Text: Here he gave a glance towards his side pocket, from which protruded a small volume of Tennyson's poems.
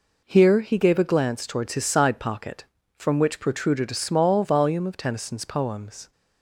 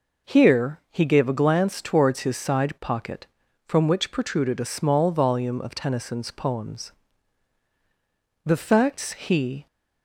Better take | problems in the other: first | goes on to say "The facts he"; noticeable; from 8.4 s on; 1.2 s long

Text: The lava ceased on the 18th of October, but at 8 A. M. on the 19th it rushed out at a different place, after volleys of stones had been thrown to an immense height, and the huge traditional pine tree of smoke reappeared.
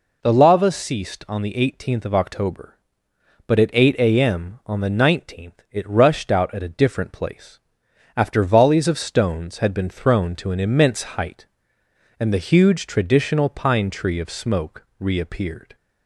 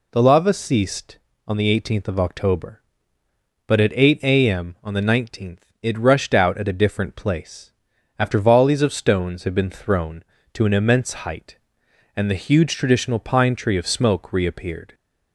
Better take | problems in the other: neither | none

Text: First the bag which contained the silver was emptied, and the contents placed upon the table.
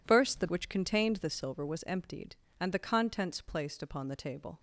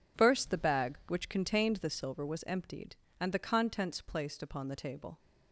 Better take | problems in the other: second | skips "bag"; at 0.4 s

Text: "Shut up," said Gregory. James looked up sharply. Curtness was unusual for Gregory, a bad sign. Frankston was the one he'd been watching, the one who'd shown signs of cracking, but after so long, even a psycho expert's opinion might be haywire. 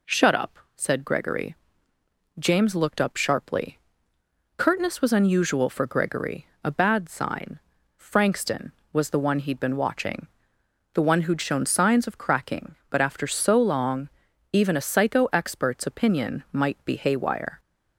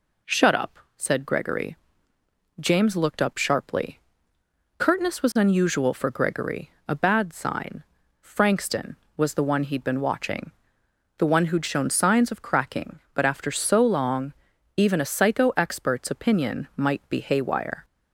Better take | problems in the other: neither | none

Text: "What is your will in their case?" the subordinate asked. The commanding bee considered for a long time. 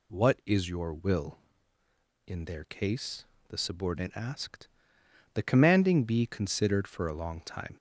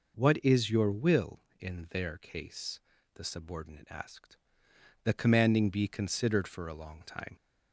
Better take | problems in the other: neither | none

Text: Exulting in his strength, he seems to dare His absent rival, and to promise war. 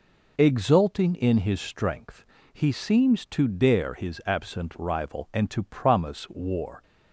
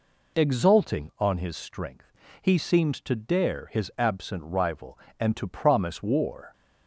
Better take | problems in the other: first | says "on" for "in"; at 1.1 s

